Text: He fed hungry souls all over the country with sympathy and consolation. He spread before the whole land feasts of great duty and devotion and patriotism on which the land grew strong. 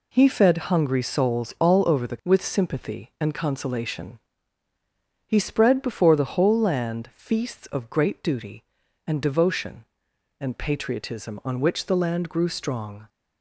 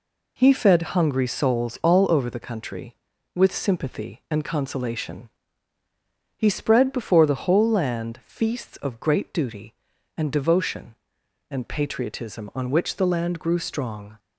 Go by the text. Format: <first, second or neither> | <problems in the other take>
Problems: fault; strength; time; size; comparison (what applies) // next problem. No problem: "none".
second | skips "country"; at 2.2 s